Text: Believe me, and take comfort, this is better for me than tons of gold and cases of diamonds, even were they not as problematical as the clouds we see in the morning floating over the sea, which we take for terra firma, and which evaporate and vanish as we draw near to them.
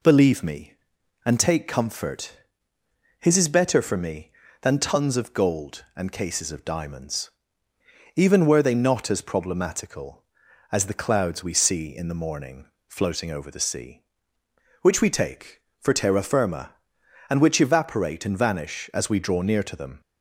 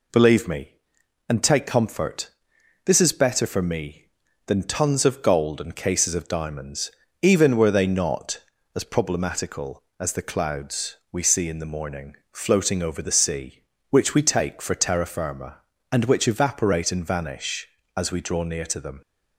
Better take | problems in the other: second | says "his" for "this"; at 3.1 s // pauses between "morning" and "floating"; slight; at 12.6 s; 0.22 s long; slight in the second

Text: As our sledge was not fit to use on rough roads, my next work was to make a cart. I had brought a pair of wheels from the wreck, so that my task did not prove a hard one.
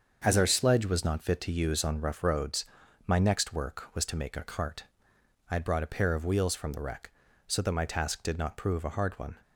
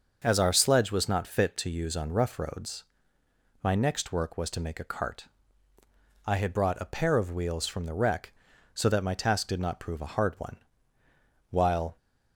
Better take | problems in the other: first | starts louder than the rest; noticeable; until 1.2 s; 6 dB; also in the first // goes on to say "While"; slight; from 11.5 s on; 0.46 s long

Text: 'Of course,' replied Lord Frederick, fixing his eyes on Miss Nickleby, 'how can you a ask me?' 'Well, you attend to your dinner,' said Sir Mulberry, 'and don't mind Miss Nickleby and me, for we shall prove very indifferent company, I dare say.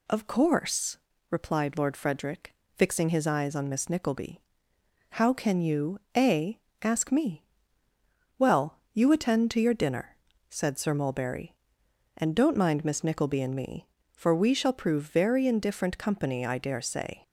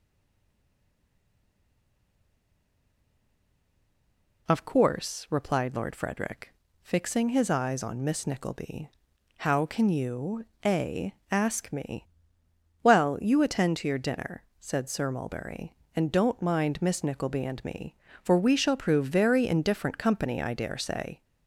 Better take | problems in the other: first | stays silent before the first word; strong; until 4.4 s; 4.4 s long // pauses between "you" and "a"; slight; at 10.4 s; 0.22 s long; slight in the first // pauses between "a" and "ask"; slight; at 11.1 s; 0.18 s long; slight in the first

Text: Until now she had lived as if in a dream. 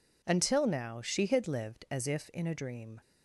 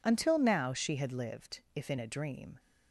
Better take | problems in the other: first | skips "as"; at 1.6 s

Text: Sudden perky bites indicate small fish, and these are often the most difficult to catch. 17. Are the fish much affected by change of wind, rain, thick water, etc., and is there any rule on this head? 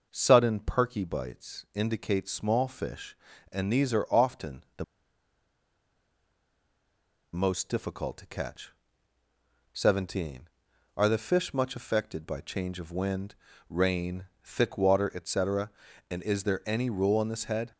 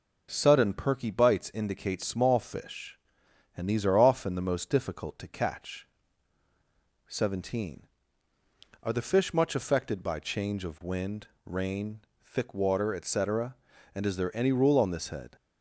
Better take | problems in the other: second | pauses between "the" and "most"; strong; at 4.8 s; 2.4 s long

